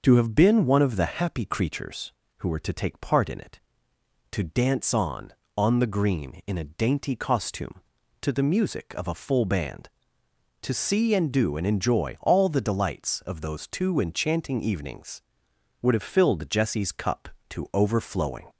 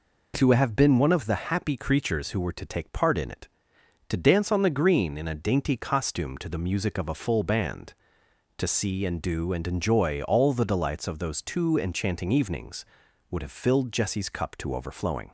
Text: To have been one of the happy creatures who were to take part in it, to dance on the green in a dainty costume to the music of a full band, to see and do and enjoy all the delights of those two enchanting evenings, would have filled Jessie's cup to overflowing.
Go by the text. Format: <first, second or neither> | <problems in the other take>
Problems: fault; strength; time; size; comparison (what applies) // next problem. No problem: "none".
second | starts louder than the rest; noticeable; until 1.0 s; 6 dB // says "on" twice; at 5.5 s